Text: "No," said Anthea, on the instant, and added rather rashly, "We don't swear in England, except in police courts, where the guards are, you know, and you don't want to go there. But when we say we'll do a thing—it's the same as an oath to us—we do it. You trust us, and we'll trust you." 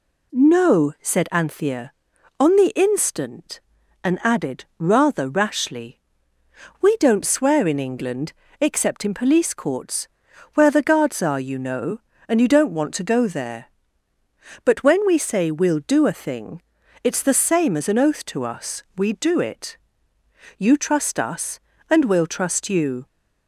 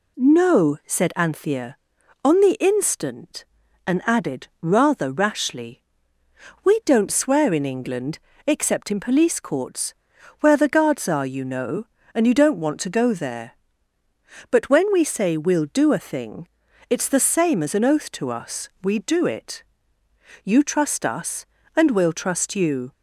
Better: neither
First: none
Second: none

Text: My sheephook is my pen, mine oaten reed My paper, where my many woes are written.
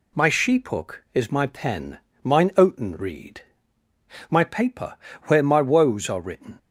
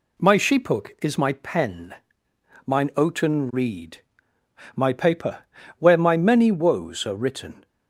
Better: second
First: pauses between "reed" and "My"; noticeable; at 3.3 s; 0.88 s long // skips "many"; at 5.6 s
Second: pauses between "reed" and "My"; noticeable; at 4.0 s; 0.74 s long

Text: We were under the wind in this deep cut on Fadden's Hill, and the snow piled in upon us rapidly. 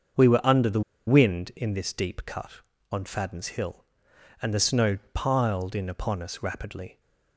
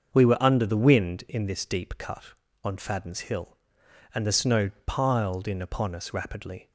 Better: second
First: starts louder than the rest; until 1.4 s; 6.5 dB // pauses between "the" and "wind"; slight; at 0.8 s; 0.26 s long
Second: starts louder than the rest; until 1.1 s; 6.5 dB

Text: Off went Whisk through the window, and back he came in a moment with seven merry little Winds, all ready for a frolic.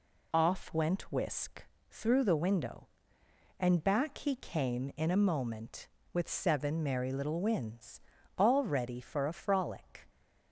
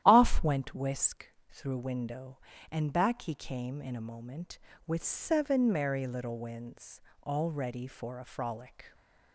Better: first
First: pauses between "Whisk" and "through"; slight; at 1.6 s; 0.24 s long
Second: starts louder than the rest; strong; until 1.0 s; 12 dB // pauses between "Whisk" and "through"; slight; at 1.2 s; 0.20 s long // skips "the"; at 1.7 s

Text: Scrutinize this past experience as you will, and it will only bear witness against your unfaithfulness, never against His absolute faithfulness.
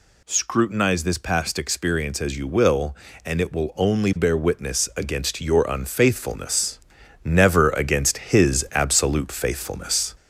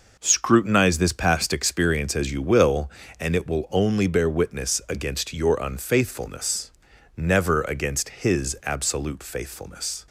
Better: second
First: gets louder; slight; throughout; 2.5 dB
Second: none

